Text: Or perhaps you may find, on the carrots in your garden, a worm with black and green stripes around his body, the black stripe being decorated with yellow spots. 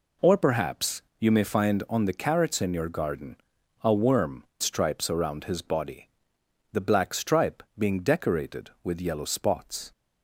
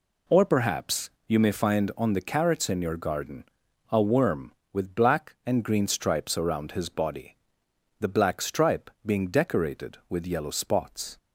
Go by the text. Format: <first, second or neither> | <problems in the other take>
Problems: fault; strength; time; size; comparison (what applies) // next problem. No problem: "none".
second | pauses between "perhaps" and "you"; slight; at 1.0 s; 0.18 s long; slight in the second // skips "with black and green"; at 4.5 s